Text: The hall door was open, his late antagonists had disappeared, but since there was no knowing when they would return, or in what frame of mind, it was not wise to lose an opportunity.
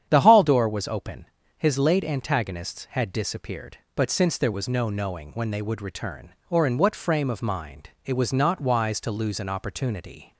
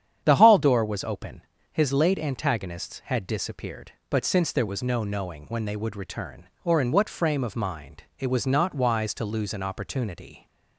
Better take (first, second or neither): neither